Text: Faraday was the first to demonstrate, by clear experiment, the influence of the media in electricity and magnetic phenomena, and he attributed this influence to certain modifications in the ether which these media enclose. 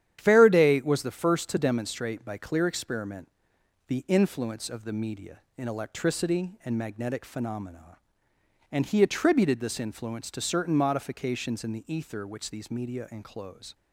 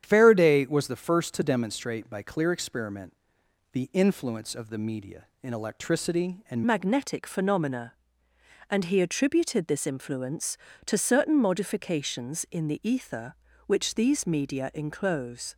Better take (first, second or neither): first